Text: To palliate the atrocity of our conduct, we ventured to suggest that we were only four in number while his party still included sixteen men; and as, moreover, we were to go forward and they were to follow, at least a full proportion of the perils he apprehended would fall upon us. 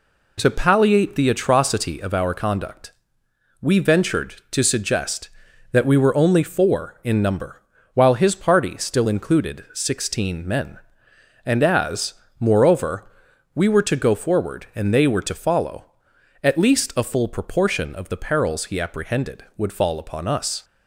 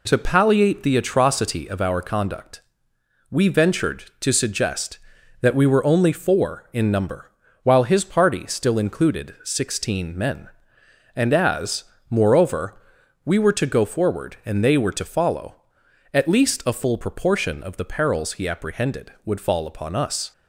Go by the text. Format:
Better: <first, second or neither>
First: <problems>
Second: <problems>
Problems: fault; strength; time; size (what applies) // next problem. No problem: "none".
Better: neither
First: pauses between "number" and "while"; slight; at 7.6 s; 0.32 s long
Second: pauses between "number" and "while"; slight; at 7.3 s; 0.32 s long